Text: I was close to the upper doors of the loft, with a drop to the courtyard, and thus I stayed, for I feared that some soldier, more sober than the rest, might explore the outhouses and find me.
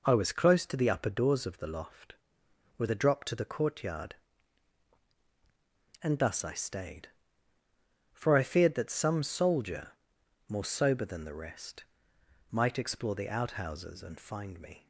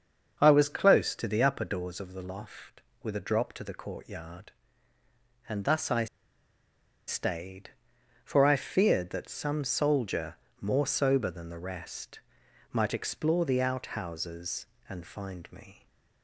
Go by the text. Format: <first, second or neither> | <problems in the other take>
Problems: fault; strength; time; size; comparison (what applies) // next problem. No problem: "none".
first | starts louder than the rest; until 1.4 s; 6.5 dB // pauses between "I" and "stayed"; at 6.0 s; 1.0 s long